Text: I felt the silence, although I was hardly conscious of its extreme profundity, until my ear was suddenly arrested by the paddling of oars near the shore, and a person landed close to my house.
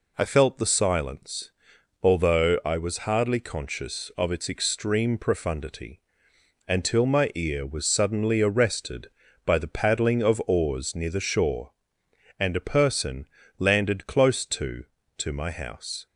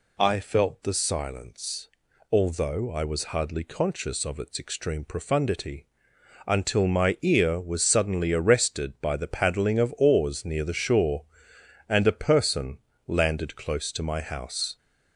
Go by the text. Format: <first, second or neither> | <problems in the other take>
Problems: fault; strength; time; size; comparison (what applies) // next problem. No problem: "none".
second | pauses between "person" and "landed"; slight; at 13.2 s; 0.32 s long; slight in the second // says "to" twice; at 15.1 s